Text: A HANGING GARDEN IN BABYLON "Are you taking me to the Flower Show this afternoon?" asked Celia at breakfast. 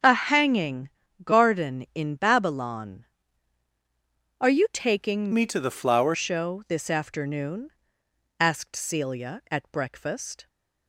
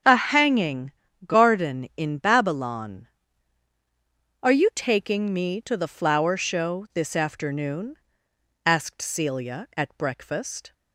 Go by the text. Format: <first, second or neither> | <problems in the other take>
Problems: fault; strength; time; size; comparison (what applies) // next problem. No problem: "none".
second | starts louder than the rest; strong; until 1.3 s; 7.5 dB; strong in the second // pauses between "HANGING" and "GARDEN"; slight; at 0.8 s; 0.34 s long; slight in the second // changes voice from "me" to "Flower"; from 5.3 to 6.1 s; 0.8 s long